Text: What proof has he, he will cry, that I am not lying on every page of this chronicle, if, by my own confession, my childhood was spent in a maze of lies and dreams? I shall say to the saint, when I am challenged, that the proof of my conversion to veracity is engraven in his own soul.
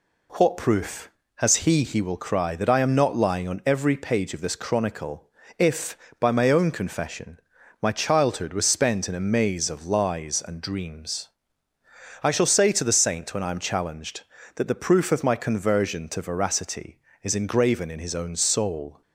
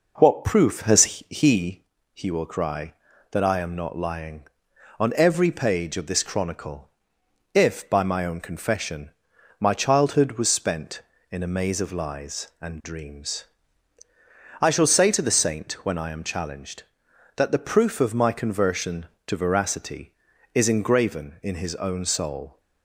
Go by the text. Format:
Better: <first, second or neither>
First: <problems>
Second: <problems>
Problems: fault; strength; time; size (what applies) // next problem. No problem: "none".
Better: first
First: none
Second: starts louder than the rest; noticeable; until 1.7 s; 5 dB